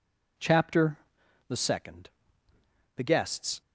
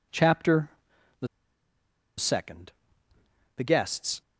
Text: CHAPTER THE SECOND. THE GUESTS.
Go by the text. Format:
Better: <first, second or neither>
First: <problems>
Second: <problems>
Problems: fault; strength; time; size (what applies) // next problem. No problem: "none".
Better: first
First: pauses between "CHAPTER" and "THE"; noticeable; at 0.9 s; 0.50 s long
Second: pauses between "CHAPTER" and "THE"; noticeable; at 0.7 s; 0.50 s long // pauses between "THE" and "SECOND"; noticeable; at 1.2 s; 0.92 s long